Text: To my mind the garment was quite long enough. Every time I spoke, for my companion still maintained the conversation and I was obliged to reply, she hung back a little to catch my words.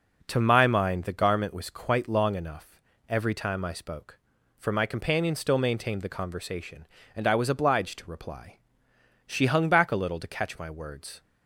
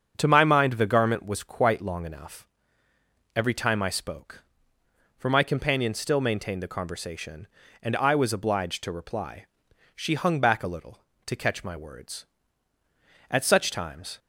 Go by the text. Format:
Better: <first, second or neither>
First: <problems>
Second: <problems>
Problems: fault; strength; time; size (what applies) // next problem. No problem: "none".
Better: first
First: none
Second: starts louder than the rest; until 1.1 s; 7 dB // goes on to say "At such times"; noticeable; from 13.2 s on; 0.90 s long